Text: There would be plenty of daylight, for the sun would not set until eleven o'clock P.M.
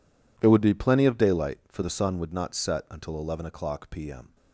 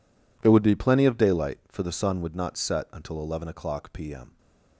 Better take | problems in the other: neither | none

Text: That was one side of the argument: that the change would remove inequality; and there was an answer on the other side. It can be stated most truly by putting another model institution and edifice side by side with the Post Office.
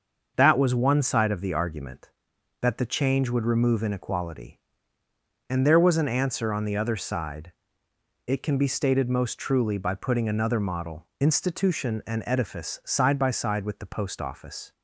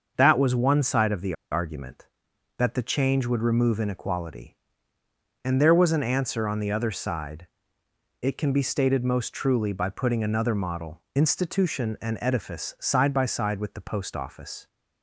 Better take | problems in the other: first | starts louder than the rest; until 1.1 s; 6.5 dB; also in the first // pauses between "the" and "argument"; slight; at 1.3 s; 0.18 s long

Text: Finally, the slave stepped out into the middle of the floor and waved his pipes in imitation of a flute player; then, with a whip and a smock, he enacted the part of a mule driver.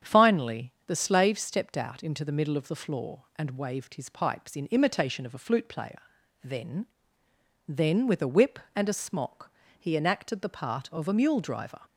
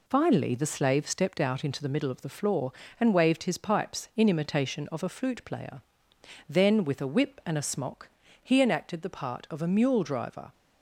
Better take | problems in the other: second | starts louder than the rest; strong; until 1.1 s; 8 dB // says "then" twice; at 7.6 s

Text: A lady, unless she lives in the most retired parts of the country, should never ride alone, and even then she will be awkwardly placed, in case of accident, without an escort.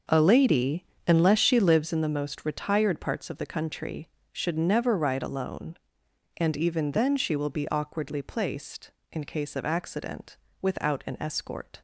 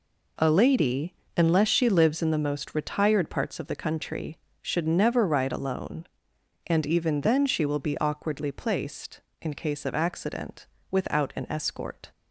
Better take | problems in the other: second | starts louder than the rest; until 1.8 s; 6.5 dB

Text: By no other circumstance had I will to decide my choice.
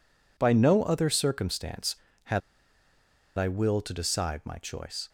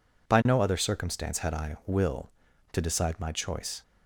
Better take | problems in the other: second | pauses between "had" and "I"; at 2.4 s; 0.98 s long

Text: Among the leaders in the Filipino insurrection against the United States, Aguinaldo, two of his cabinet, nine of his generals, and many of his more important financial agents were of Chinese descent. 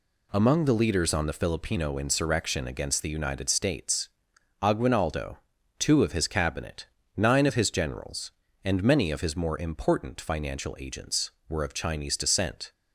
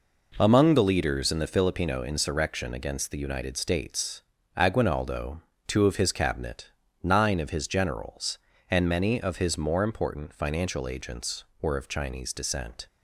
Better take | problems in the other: second | says "on" for "in"; at 1.1 s

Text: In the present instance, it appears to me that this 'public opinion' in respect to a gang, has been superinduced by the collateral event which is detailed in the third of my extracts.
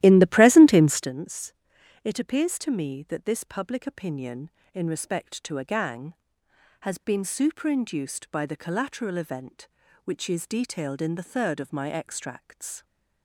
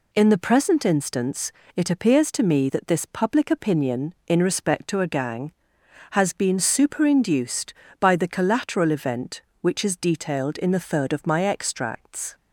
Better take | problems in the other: second | starts louder than the rest; strong; until 1.1 s; 14 dB

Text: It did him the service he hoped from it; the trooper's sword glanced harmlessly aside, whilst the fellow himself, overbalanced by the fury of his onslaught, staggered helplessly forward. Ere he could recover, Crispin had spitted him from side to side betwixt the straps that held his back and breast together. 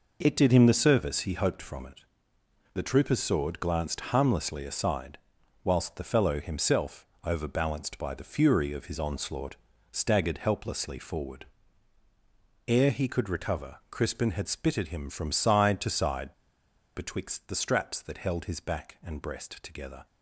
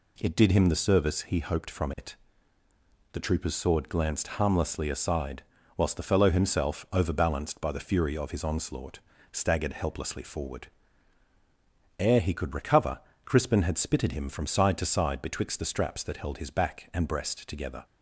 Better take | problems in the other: second | pauses between "side" and "betwixt"; noticeable; at 16.3 s; 0.61 s long

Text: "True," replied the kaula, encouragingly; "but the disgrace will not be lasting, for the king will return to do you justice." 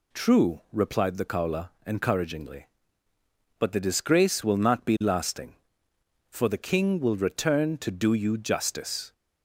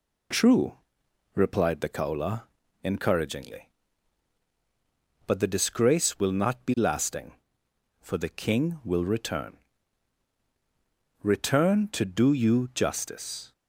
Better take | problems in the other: first | says "return" twice; at 11.2 s

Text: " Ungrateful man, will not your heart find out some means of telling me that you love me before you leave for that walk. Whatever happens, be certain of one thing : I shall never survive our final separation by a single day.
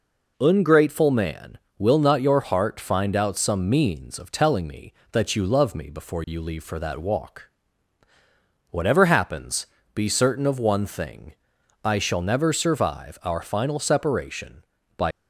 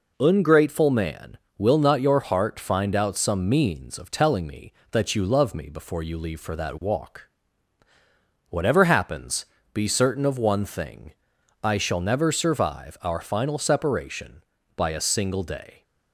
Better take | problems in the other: second | stops before "a single day"; at 15.1 s

